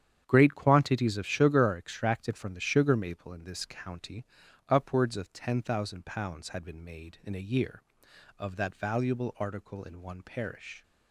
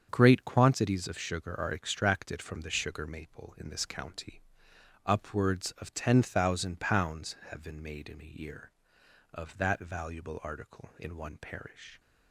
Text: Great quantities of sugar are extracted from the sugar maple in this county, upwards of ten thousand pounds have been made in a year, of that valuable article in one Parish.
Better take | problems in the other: second | starts louder than the rest; strong; until 1.2 s; 9 dB; also in the second // says "had" for "have"; at 6.4 s

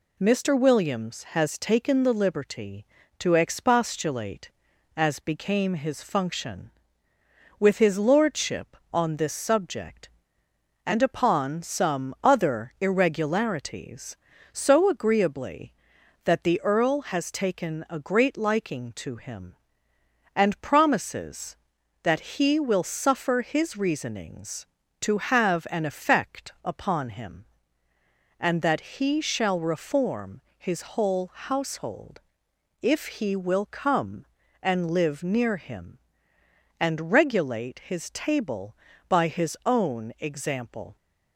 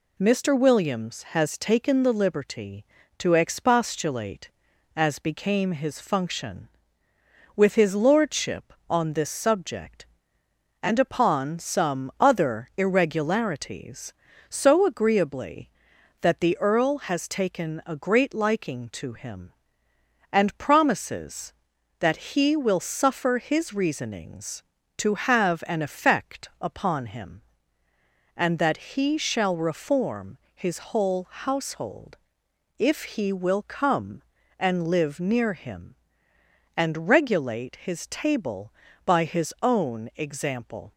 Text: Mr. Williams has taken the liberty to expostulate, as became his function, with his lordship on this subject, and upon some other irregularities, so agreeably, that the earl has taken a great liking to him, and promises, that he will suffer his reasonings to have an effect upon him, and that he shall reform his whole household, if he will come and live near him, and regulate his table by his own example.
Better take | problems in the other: neither | pauses between "reform" and "his"; slight; the same in both

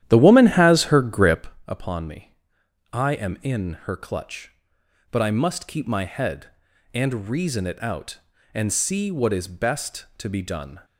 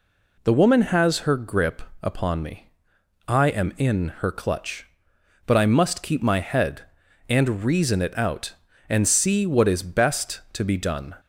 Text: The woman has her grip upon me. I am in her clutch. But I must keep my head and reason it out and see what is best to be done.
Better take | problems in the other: second | starts louder than the rest; strong; until 1.5 s; 11.5 dB // pauses between "grip" and "upon"; slight; at 1.4 s; 0.18 s long; slight in the second

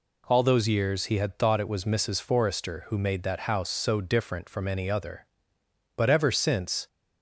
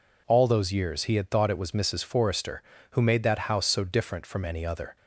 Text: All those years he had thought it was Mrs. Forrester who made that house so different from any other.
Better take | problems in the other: second | goes on to say "But ever since"; noticeable; from 5.9 s on; 0.90 s long

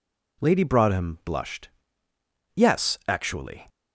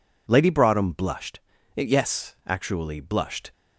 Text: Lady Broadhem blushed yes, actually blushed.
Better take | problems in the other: second | pauses between "blushed" and "yes"; noticeable; at 1.6 s; 0.86 s long; slight in the second // stops before "blushed"; at 3.6 s

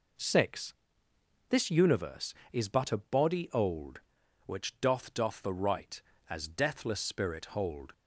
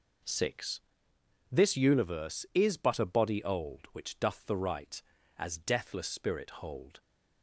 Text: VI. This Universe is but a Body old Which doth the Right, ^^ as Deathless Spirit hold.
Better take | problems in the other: second | says "doth" twice; at 5.1 s

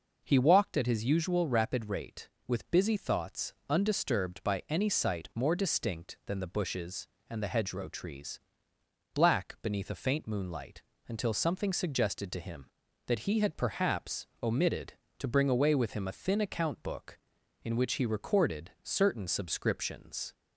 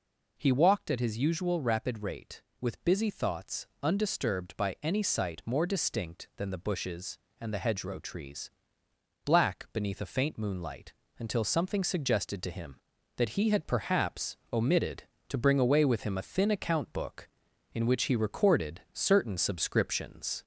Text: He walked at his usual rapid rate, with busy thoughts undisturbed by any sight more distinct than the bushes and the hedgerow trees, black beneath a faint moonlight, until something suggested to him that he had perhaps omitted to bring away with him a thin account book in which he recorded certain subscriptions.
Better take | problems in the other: first | gets louder; slight; throughout; 2 dB // pauses between "thoughts" and "undisturbed"; slight; at 3.6 s; 0.16 s long; slight in the first // pauses between "perhaps" and "omitted"; slight; at 14.3 s; 0.16 s long; slight in the first

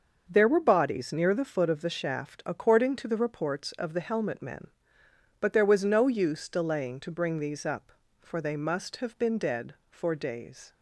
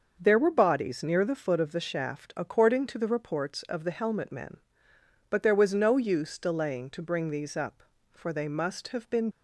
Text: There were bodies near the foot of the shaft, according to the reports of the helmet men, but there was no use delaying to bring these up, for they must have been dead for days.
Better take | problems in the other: first | starts louder than the rest; until 1.2 s; 6 dB; also in the first // stops before "dead for days"; at 9.3 s

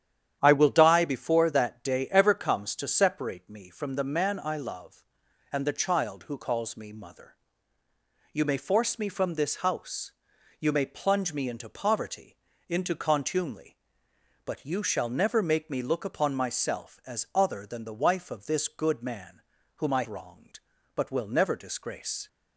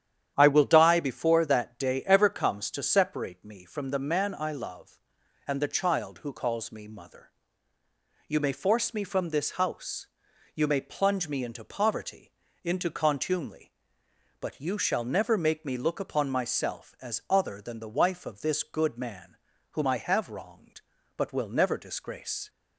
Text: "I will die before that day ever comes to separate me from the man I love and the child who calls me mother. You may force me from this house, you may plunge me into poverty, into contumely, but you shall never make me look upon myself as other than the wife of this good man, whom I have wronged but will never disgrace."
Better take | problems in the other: second | starts louder than the rest; strong; until 1.4 s; 9.5 dB; strong in the second // skips "have"; at 20.0 s

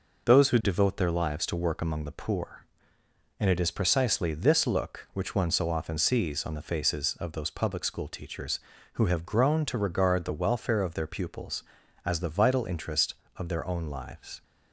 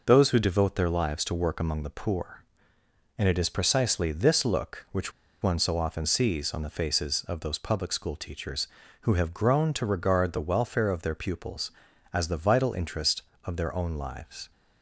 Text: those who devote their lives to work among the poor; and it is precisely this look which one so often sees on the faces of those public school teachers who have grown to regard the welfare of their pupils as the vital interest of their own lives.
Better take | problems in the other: first | pauses between "which" and "one"; slight; at 5.1 s; 0.30 s long

